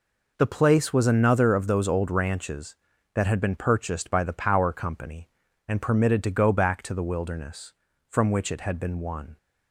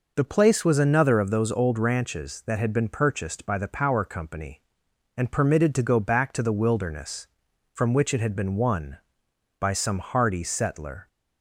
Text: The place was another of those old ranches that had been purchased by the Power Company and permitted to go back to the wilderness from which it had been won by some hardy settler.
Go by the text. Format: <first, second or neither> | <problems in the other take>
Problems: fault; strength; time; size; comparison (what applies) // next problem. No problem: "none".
second | stops before "by some hardy settler"; at 9.3 s